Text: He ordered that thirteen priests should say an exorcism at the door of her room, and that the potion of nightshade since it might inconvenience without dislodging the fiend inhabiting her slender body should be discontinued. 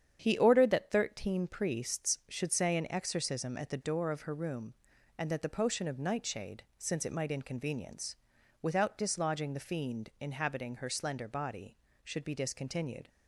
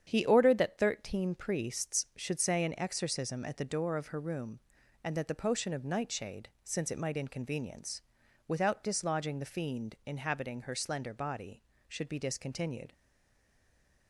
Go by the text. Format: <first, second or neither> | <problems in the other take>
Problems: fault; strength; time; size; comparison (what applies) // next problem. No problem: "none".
first | starts louder than the rest; strong; until 1.0 s; 8.5 dB; strong in the first // pauses between "nightshade" and "since"; slight; at 6.4 s; 0.16 s long; slight in the first // pauses between "inconvenience" and "without"; noticeable; at 7.9 s; 0.48 s long; noticeable in the first // stays silent after the last word; noticeable; from 12.9 s on; 1.1 s long